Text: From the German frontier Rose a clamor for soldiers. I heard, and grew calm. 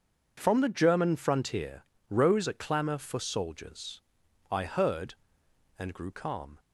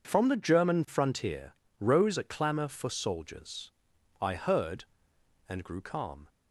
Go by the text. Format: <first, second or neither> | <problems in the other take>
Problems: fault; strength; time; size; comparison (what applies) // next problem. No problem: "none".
neither | pauses between "frontier" and "Rose"; slight; the same in both